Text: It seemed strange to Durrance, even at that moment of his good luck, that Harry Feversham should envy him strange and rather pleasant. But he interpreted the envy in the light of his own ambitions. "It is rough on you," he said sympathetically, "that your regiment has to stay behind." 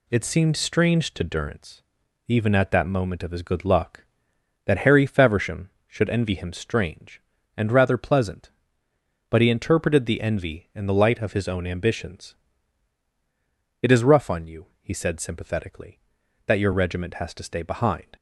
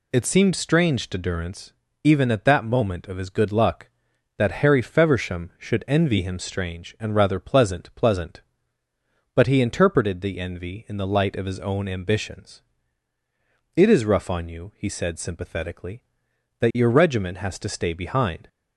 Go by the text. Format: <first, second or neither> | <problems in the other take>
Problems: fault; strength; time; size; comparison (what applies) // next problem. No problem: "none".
first | says "pleasant" twice; at 7.9 s